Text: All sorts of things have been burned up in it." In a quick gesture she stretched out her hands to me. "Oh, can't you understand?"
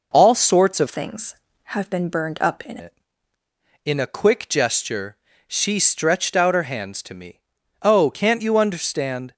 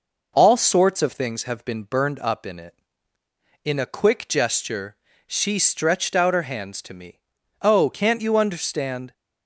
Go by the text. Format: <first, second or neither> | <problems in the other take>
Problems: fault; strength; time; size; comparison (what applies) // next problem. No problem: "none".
second | changes voice from "things" to "in"; from 0.8 to 2.7 s; 1.9 s long // pauses between "gesture" and "she"; slight; at 5.1 s; 0.32 s long; slight in the second